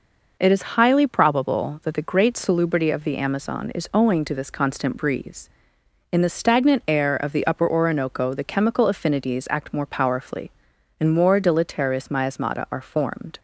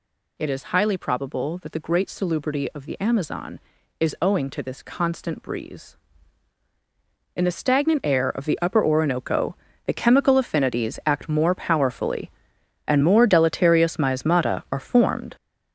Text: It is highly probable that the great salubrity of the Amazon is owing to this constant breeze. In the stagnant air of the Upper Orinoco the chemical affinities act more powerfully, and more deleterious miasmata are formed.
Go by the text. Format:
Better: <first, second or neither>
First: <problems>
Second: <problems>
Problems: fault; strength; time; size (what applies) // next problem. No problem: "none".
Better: first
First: none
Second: gets louder; strong; throughout; 8 dB // pauses between "Orinoco" and "the"; slight; at 9.5 s; 0.30 s long